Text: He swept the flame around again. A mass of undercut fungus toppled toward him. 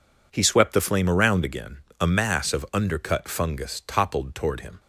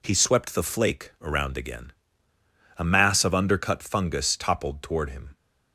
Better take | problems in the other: first | says "flake" for "flame"; at 0.6 s

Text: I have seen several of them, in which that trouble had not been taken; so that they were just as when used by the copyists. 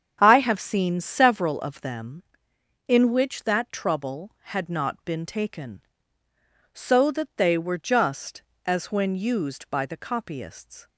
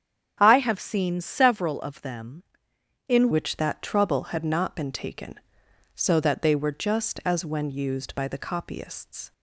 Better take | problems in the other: first | starts louder than the rest; strong; until 1.4 s; 8.5 dB; strong in the first // changes voice at "which"; from 3.3 s on; 6.0 s long

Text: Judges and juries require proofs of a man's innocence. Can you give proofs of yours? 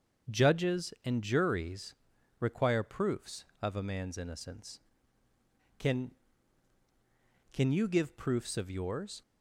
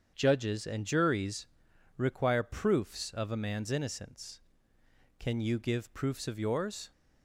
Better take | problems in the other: second | starts louder than the rest; strong; until 1.4 s; 7 dB; strong in the second // pauses between "juries" and "require"; noticeable; at 1.9 s; 0.46 s long; noticeable in the second // says "Can" twice; at 7.5 s

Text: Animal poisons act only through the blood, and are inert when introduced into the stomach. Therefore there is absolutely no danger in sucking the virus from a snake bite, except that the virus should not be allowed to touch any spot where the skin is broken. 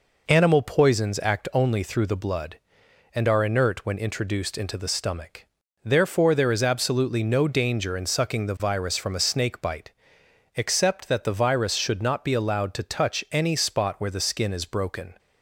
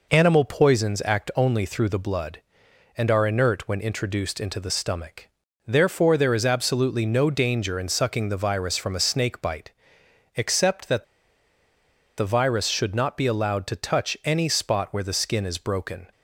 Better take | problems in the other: first | pauses between "that" and "the"; at 11.0 s; 1.1 s long

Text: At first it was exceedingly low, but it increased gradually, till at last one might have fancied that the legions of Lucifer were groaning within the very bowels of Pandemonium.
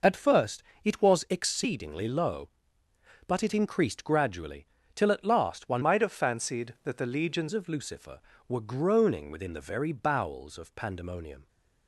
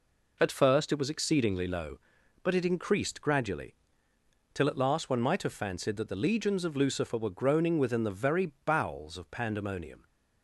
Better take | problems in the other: second | pauses between "first" and "it"; slight; at 0.6 s; 0.22 s long // changes voice from "might" to "legions"; from 5.8 to 7.4 s; 1.6 s long

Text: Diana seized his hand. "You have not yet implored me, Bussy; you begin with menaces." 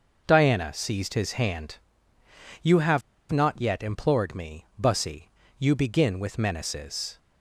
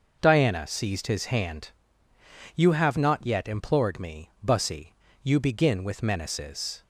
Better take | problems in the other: second | pauses between "have" and "not"; slight; at 3.0 s; 0.30 s long

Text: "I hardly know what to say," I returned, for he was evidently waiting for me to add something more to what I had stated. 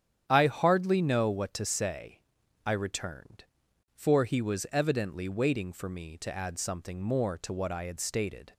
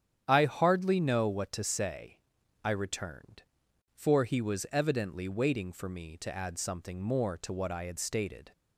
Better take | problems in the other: neither | starts louder than the rest; strong; the same in both

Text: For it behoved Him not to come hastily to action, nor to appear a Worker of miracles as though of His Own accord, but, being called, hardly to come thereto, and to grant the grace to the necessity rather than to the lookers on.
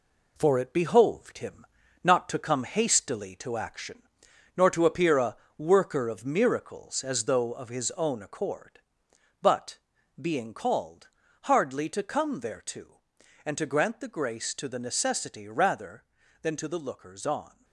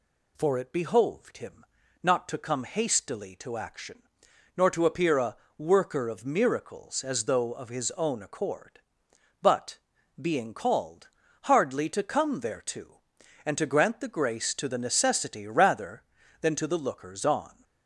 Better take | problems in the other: second | gets quieter; throughout; 6 dB // pauses between "Him" and "not"; at 1.6 s; 0.38 s long; also in the second // pauses between "a" and "Worker"; slight; at 5.3 s; 0.22 s long; slight in the second

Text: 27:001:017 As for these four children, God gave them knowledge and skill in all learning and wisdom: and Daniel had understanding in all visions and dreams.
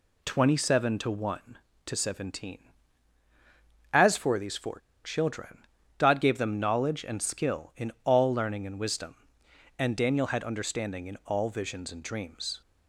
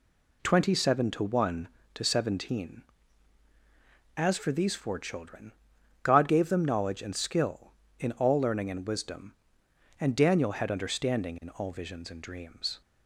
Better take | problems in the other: second | pauses between "four" and "children"; slight; at 4.7 s; 0.25 s long

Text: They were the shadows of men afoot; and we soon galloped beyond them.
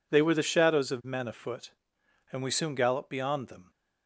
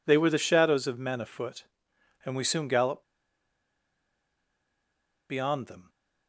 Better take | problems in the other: first | pauses between "galloped" and "beyond"; strong; at 3.0 s; 2.2 s long

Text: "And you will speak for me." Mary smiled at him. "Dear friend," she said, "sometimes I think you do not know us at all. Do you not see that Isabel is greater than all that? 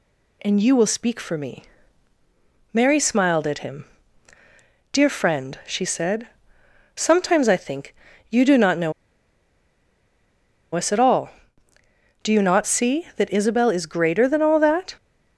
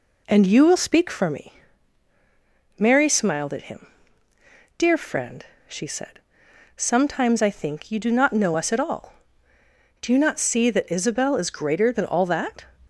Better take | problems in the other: second | pauses between "think" and "you"; slight; at 7.9 s; 0.36 s long // pauses between "know" and "us"; strong; at 8.9 s; 1.8 s long

